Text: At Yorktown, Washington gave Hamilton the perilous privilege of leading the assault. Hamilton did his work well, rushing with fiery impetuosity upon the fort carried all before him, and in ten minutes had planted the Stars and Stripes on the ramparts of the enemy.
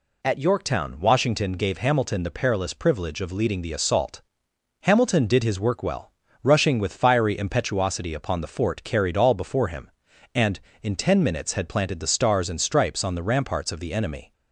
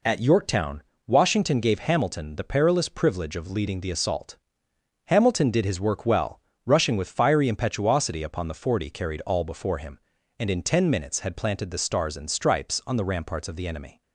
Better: first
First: none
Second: says "forty" for "fort"; at 8.5 s

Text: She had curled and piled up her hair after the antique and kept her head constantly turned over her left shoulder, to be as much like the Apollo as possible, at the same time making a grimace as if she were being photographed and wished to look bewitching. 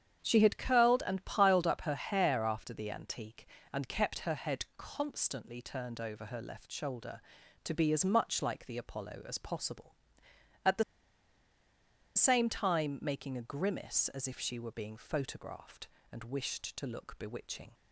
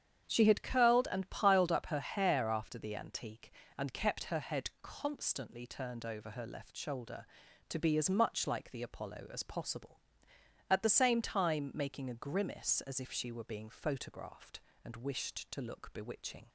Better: second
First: starts louder than the rest; strong; until 1.2 s; 8.5 dB // pauses between "the" and "same"; strong; at 10.8 s; 1.3 s long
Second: starts louder than the rest; strong; until 1.2 s; 8.5 dB

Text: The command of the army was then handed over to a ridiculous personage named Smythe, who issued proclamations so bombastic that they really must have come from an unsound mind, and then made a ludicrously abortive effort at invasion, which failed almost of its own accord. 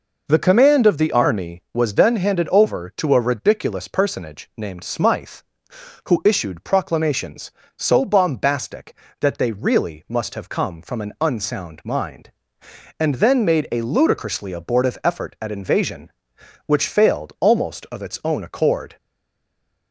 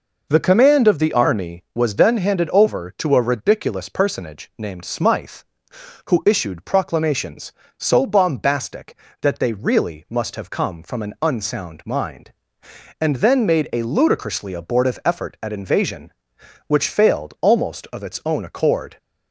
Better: second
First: stays silent after the last word; slight; from 18.9 s on; 1.0 s long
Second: none

